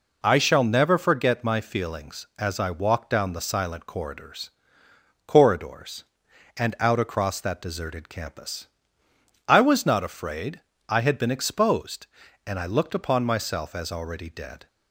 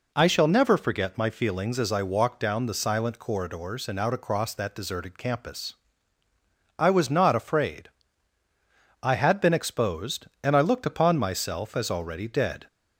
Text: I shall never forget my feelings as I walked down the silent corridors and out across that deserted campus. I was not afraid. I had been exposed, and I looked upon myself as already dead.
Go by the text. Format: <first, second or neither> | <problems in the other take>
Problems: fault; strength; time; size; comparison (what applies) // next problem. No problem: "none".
second | says "corridors" twice; at 5.2 s